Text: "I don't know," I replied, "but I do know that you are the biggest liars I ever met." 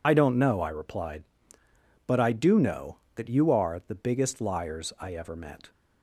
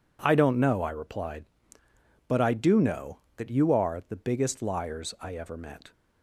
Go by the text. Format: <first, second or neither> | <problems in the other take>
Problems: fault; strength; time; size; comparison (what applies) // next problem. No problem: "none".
second | loses the start of "I"; at 0.0 s; 70 ms